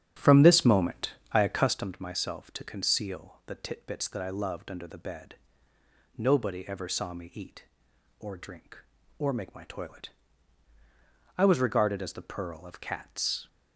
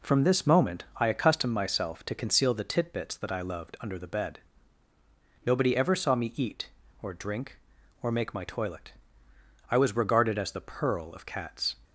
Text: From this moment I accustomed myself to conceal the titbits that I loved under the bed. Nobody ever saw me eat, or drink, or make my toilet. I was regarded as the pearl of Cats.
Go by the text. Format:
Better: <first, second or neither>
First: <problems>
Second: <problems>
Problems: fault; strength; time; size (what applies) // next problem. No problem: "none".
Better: second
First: starts louder than the rest; strong; until 1.8 s; 9.5 dB // pauses between "moment" and "I"; slight; at 1.1 s; 0.18 s long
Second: none